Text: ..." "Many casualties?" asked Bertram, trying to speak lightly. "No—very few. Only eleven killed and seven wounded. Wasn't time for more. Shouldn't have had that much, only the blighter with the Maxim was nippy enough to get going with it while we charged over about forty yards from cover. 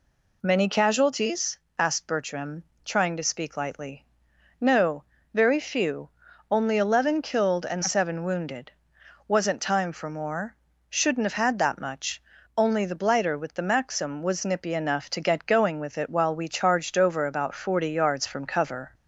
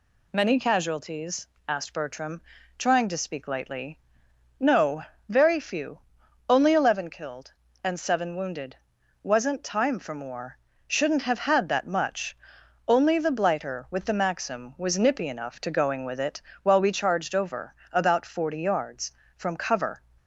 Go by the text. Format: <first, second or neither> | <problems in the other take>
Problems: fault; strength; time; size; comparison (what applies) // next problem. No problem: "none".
first | skips "get"; at 15.7 s // pauses between "it" and "while"; slight; at 16.4 s; 0.20 s long // pauses between "over" and "about"; slight; at 17.7 s; 0.18 s long